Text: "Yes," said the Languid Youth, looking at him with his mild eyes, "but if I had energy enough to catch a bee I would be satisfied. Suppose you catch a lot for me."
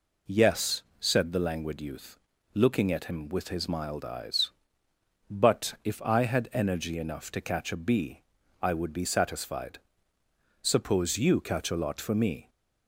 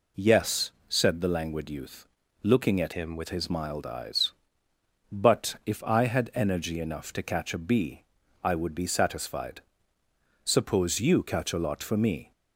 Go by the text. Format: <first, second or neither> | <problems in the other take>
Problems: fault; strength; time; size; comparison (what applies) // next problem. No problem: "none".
first | changes voice from "him" to "with"; from 2.9 to 3.2 s; 0.3 s long // pauses between "bee" and "I"; at 8.0 s; 0.38 s long; also in the first